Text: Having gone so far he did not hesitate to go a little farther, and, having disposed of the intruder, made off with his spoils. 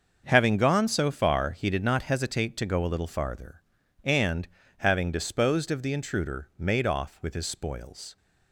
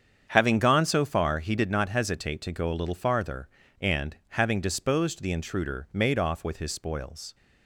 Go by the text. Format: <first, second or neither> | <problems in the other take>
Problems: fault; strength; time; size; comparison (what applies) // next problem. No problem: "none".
first | starts louder than the rest; strong; until 1.3 s; 7.5 dB; also in the first // skips "of"; at 5.2 s